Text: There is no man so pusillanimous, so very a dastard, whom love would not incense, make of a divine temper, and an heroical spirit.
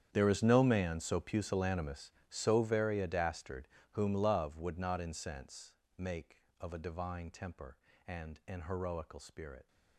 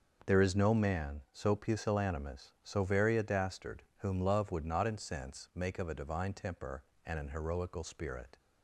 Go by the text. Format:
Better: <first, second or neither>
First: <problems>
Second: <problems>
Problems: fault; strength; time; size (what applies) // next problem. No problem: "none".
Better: second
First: gets quieter; strong; throughout; 17.5 dB // starts louder than the rest; strong; until 1.1 s; 9 dB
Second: starts louder than the rest; noticeable; until 1.3 s; 6 dB